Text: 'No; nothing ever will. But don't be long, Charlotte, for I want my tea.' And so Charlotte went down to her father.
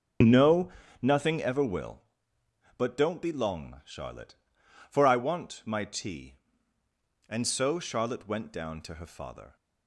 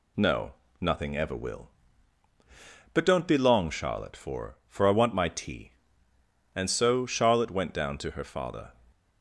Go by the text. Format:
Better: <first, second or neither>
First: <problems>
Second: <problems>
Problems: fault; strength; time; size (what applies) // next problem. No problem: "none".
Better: first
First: none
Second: says "for" twice; at 4.6 s